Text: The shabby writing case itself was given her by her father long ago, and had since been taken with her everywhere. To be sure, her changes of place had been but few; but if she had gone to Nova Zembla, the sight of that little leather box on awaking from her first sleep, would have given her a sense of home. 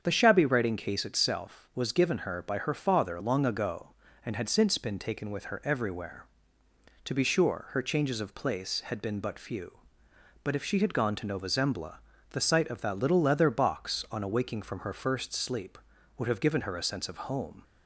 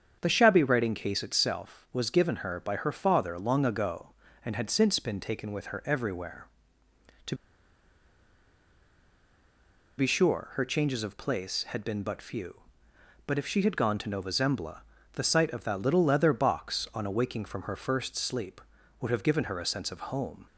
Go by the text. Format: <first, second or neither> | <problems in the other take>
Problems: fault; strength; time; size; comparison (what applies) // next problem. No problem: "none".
first | starts louder than the rest; strong; until 1.2 s; 7.5 dB; strong in the first // pauses between "To" and "be"; strong; at 7.3 s; 2.6 s long